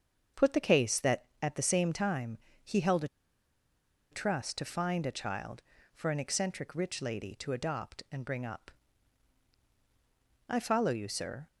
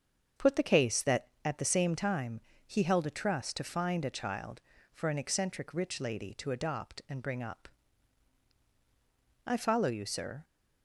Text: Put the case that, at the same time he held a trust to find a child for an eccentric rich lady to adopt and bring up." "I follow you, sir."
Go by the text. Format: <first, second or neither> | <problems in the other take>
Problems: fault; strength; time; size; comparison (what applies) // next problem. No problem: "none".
second | starts louder than the rest; until 1.5 s; 7 dB; also in the second // pauses between "time" and "he"; slight; at 2.3 s; 0.26 s long; slight in the second // pauses between "a" and "trust"; at 3.0 s; 1.0 s long